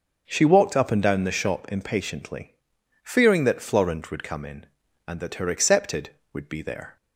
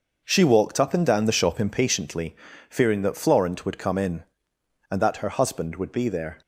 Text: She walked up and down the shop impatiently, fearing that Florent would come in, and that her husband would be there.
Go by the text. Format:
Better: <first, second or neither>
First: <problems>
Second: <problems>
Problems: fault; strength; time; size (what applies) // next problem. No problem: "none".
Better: second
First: starts louder than the rest; until 1.2 s; 6.5 dB // says "accepted" for "husband"; at 5.4 s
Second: none